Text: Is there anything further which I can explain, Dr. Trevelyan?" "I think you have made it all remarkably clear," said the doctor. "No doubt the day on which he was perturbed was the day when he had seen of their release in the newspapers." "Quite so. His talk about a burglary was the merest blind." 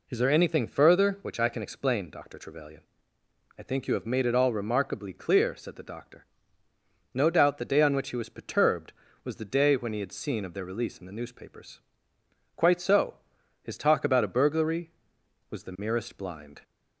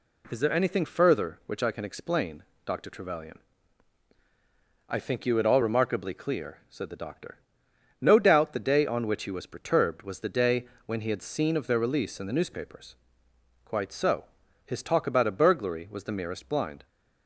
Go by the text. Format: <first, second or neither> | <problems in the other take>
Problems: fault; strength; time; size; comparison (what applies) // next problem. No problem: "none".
first | skips "have made"; at 5.3 s // pauses between "day" and "when"; slight; at 10.6 s; 0.22 s long